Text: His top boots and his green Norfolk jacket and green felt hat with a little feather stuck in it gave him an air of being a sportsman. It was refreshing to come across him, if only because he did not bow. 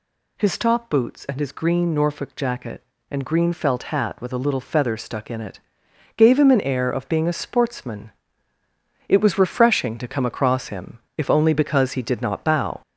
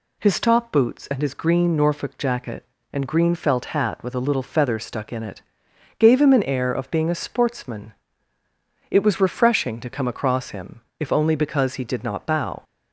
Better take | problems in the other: second | gets louder; noticeable; throughout; 4.5 dB // pauses between "it" and "gave"; noticeable; at 5.5 s; 0.56 s long; noticeable in the second

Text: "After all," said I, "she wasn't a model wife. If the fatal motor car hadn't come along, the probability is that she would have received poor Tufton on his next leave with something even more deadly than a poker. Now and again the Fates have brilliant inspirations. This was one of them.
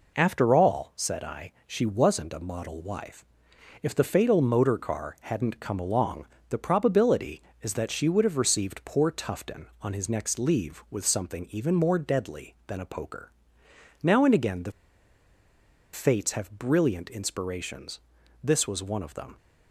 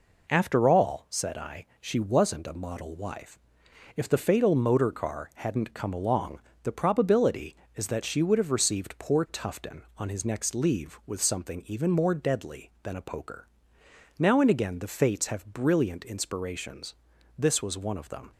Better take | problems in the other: second | pauses between "the" and "Fates"; at 14.7 s; 1.2 s long

